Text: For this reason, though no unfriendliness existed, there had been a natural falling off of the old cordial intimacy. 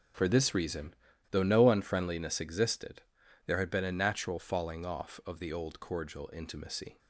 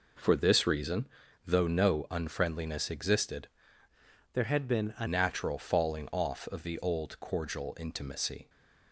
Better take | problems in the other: first | changes voice from "there" to "a"; from 4.3 to 5.0 s; 0.7 s long

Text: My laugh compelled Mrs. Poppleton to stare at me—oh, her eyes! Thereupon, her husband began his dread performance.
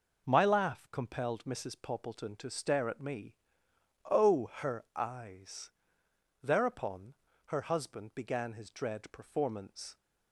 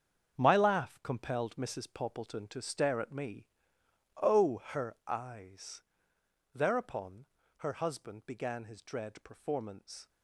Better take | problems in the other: first | gets quieter; strong; throughout; 11.5 dB

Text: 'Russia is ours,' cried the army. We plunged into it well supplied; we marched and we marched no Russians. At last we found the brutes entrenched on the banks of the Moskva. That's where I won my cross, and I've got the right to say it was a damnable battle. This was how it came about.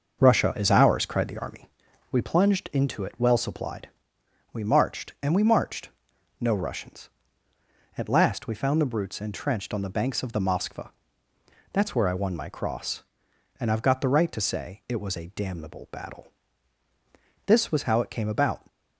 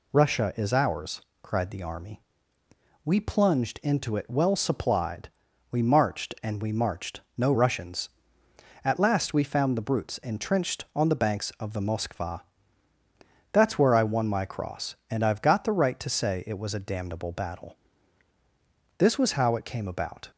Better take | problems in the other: second | starts louder than the rest; until 1.7 s; 6.5 dB // pauses between "marched" and "no"; noticeable; at 5.9 s; 0.50 s long; slight in the second

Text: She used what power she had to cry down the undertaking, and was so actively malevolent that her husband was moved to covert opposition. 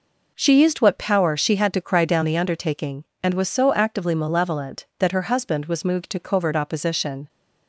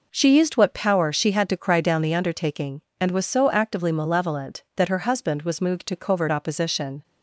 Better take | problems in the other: neither | none

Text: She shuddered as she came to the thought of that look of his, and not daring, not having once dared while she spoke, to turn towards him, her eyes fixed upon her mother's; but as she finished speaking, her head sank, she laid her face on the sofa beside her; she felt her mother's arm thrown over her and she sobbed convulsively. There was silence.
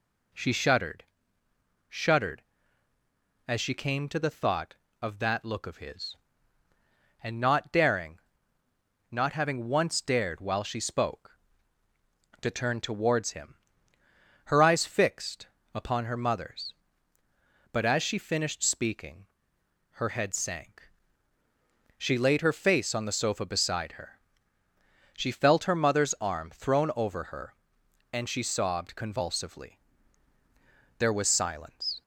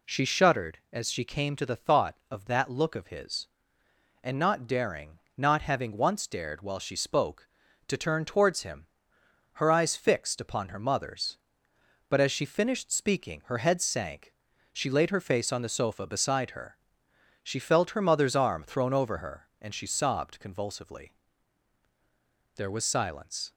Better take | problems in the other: second | says "shuddered" twice; at 1.9 s // pauses between "fixed" and "upon"; slight; at 15.4 s; 0.26 s long

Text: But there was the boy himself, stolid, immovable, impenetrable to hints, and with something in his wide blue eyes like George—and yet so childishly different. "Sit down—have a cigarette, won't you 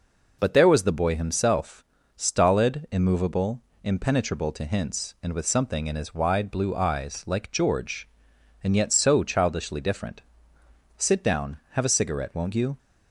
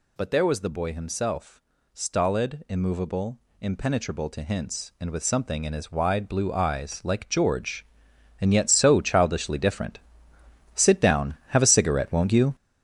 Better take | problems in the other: first | gets louder; strong; throughout; 9 dB

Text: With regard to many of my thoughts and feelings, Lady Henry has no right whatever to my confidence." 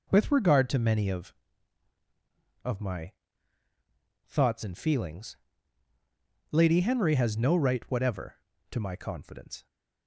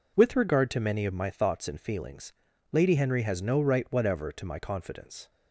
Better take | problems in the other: second | says "of" twice; at 2.6 s // pauses between "my" and "thoughts"; at 3.1 s; 1.1 s long

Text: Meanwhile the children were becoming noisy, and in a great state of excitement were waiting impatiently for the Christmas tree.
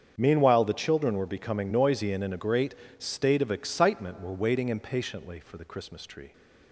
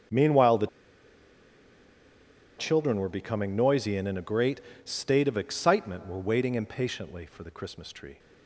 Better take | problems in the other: first | starts louder than the rest; strong; until 3.0 s; 7.5 dB; strong in the first // pauses between "the" and "children"; strong; at 0.6 s; 1.9 s long // pauses between "great" and "state"; slight; at 4.6 s; 0.22 s long; slight in the first

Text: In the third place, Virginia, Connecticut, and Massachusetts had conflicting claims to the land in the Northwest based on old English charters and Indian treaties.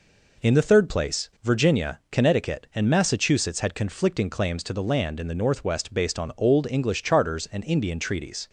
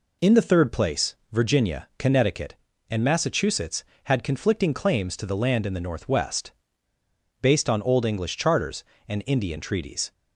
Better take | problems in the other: first | pauses between "Northwest" and "based"; noticeable; at 6.5 s; 0.91 s long

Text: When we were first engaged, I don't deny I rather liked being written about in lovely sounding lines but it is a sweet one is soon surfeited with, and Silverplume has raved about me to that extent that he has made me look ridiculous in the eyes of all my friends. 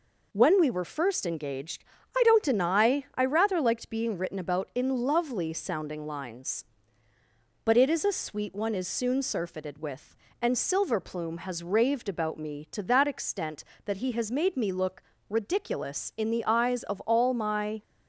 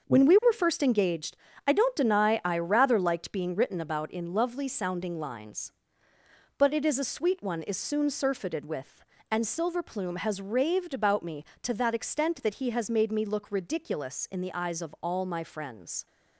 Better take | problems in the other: second | pauses between "look" and "ridiculous"; slight; at 15.0 s; 0.26 s long // stops before "friends"; at 17.8 s

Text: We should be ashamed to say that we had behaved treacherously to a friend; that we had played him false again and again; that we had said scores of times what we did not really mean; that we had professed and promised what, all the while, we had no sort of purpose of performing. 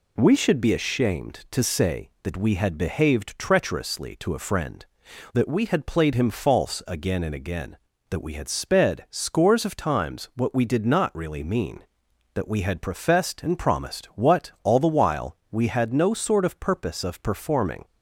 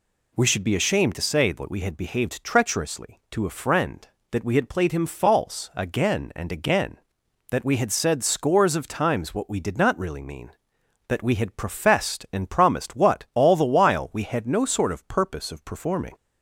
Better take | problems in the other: second | says "sped" for "said"; at 8.4 s

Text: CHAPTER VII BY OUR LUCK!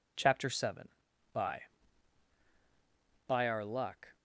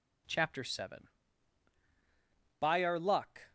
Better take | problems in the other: second | says "BY" twice; at 3.2 s

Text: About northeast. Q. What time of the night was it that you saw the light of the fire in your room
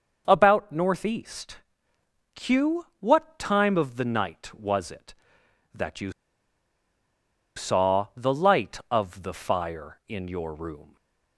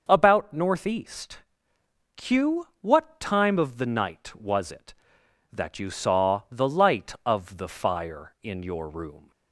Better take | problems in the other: second | starts louder than the rest; noticeable; until 1.2 s; 6 dB; noticeable in the second // pauses between "you" and "saw"; strong; at 6.0 s; 1.4 s long // stays silent after the last word; slight; from 10.8 s on; 0.5 s long

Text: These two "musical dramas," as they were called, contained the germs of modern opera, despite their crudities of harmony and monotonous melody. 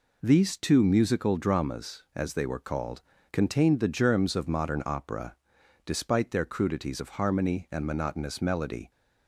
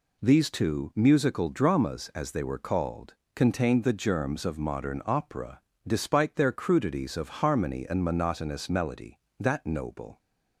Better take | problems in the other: first | goes on to say "That noble"; noticeable; from 9.3 s on; 0.80 s long

